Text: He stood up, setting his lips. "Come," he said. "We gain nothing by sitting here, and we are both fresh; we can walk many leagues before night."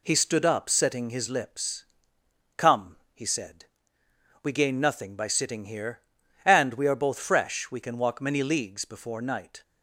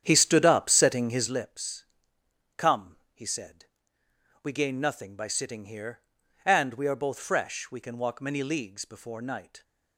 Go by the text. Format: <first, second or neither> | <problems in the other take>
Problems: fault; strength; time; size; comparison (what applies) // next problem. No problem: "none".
first | starts louder than the rest; strong; until 1.5 s; 9 dB